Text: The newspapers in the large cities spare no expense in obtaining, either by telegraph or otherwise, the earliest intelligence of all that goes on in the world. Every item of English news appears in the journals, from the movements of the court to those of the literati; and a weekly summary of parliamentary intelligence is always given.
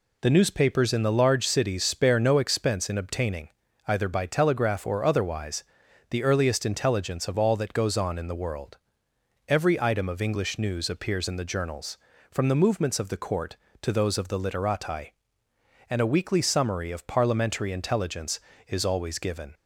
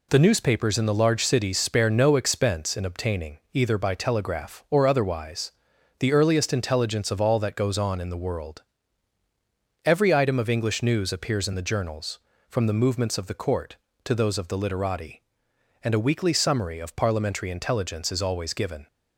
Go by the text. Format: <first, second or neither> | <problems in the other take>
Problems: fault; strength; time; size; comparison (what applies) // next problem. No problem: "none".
neither | none